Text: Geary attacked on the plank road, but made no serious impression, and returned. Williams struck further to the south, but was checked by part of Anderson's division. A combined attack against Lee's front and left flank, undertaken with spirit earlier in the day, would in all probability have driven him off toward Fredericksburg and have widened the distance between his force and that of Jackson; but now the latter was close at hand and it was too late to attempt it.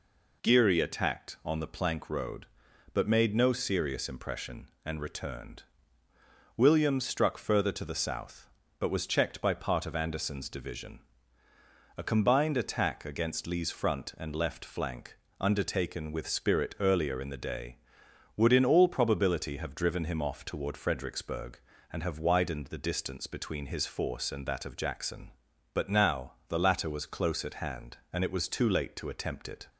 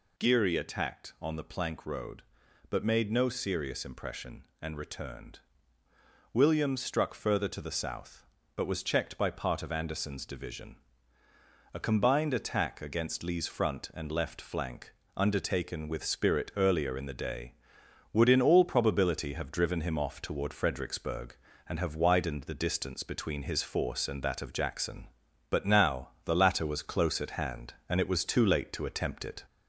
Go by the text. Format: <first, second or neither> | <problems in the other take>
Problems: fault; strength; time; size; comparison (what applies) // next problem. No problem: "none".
first | gets louder; slight; throughout; 2 dB // pauses between "now" and "the"; slight; at 26.0 s; 0.16 s long; slight in the first